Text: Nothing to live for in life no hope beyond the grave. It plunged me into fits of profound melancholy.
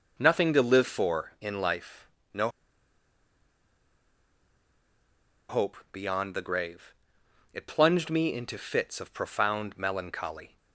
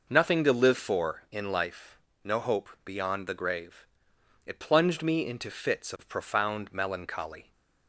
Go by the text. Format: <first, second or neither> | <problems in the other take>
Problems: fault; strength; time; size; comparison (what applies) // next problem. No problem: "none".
second | pauses between "life" and "no"; slight; at 2.0 s; 0.26 s long; slight in the second // pauses between "no" and "hope"; strong; at 2.4 s; 3.0 s long // pauses between "hope" and "beyond"; slight; at 5.7 s; 0.16 s long; slight in the second